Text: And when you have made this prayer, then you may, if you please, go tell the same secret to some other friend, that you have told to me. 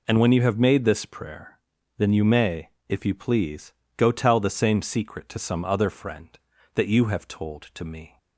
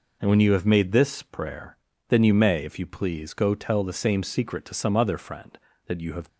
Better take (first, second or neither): first